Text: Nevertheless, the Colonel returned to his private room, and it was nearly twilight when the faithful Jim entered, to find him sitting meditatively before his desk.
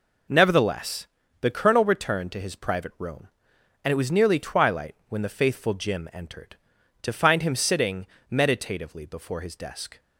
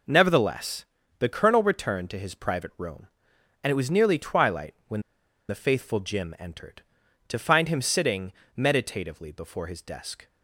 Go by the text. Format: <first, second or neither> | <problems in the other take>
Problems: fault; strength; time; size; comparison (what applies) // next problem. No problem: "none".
first | pauses between "when" and "the"; noticeable; at 5.0 s; 0.47 s long // pauses between "sitting" and "meditatively"; slight; at 8.3 s; 0.24 s long; slight in the first